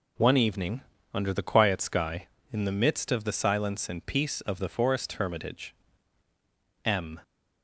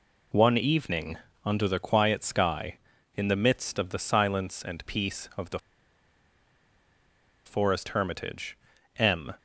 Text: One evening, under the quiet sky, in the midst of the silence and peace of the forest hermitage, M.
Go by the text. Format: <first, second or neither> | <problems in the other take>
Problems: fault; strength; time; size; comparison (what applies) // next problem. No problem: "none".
first | pauses between "the" and "forest"; strong; at 5.5 s; 1.8 s long